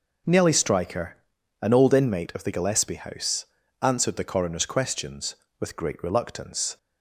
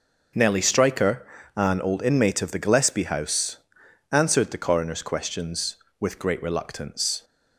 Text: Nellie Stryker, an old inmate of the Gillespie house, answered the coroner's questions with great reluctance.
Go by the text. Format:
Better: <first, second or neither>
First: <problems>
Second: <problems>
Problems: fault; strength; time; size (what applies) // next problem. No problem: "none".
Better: neither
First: none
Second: none